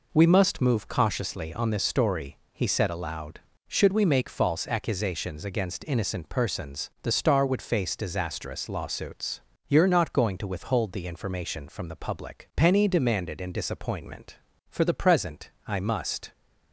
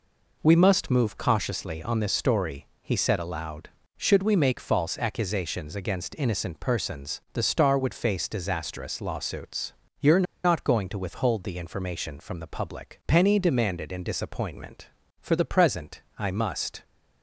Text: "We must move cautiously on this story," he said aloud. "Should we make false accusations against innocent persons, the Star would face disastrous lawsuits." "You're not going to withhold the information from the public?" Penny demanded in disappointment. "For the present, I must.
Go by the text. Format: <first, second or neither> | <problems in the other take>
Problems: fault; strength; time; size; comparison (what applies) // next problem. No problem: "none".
first | pauses between "You're" and "not"; slight; at 10.2 s; 0.21 s long